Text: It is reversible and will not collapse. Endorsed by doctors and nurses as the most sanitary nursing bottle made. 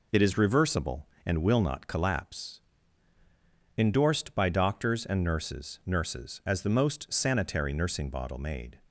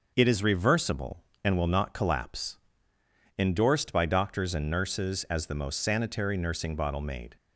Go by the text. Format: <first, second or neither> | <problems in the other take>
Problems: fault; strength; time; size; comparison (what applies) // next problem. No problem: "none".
second | says "nurses" twice; at 5.8 s